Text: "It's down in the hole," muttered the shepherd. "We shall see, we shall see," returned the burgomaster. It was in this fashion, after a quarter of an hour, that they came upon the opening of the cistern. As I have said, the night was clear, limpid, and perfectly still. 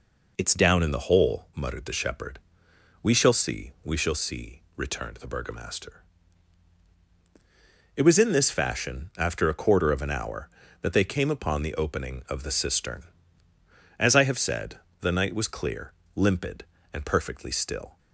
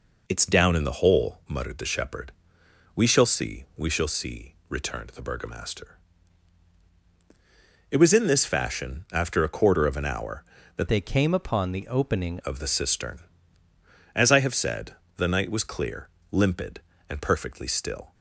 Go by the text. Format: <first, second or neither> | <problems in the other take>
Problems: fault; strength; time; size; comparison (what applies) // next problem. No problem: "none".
first | changes voice from "they" to "opening"; from 10.8 to 12.3 s; 1.5 s long